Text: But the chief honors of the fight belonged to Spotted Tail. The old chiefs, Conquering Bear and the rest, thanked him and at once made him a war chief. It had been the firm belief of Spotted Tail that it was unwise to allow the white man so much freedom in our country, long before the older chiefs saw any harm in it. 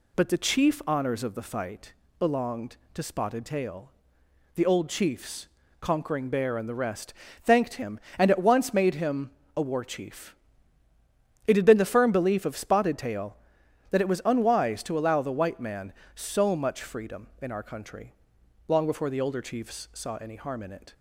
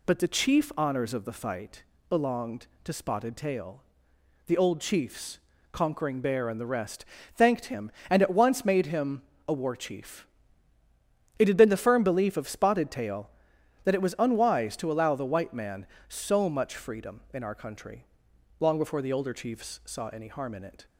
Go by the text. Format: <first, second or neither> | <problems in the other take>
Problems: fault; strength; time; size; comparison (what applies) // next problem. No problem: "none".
neither | pauses between "fight" and "belonged"; slight; the same in both // pauses between "him" and "a"; slight; the same in both